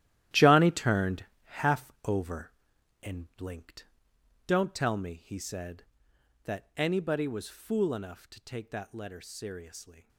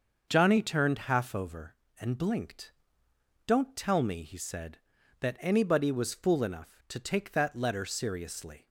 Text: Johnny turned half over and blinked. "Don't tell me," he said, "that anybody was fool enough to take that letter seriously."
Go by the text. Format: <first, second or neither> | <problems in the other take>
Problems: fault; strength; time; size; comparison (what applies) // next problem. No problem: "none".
second | gets quieter; strong; throughout; 12.5 dB // starts louder than the rest; strong; until 1.5 s; 13 dB; also in the second // pauses between "turned" and "half"; slight; at 1.2 s; 0.20 s long